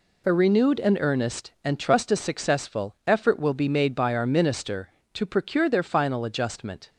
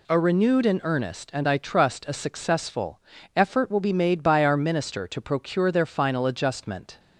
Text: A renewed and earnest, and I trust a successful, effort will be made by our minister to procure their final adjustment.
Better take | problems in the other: second | skips "I"; at 1.7 s

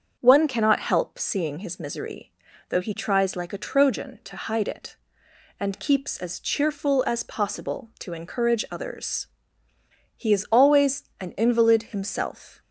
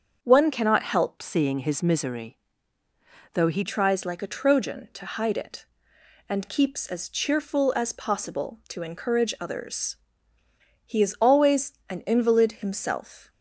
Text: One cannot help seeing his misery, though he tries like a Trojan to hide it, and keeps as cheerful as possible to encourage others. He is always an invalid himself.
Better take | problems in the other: first | starts louder than the rest; until 1.2 s; 7 dB; also in the first // changes voice from "seeing" to "he"; from 1.2 to 3.6 s; 2.4 s long // pauses between "always" and "an"; slight; at 11.7 s; 0.16 s long; slight in the first

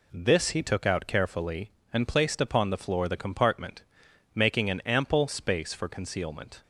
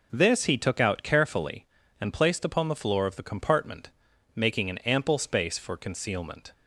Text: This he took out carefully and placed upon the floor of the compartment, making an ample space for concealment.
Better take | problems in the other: second | skips "of"; at 3.0 s

